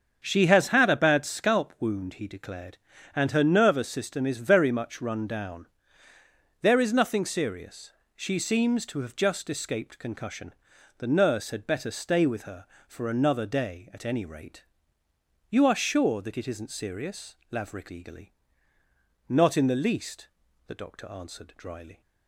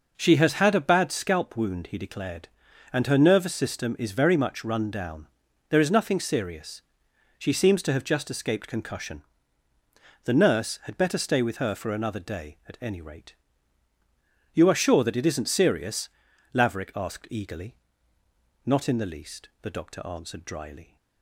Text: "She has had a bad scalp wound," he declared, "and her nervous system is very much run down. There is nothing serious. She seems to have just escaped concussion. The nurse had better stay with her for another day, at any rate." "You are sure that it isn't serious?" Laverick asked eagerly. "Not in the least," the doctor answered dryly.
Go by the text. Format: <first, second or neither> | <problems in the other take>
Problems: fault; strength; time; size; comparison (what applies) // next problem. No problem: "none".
second | starts louder than the rest; strong; until 1.2 s; 7 dB // skips "asked"; at 17.8 s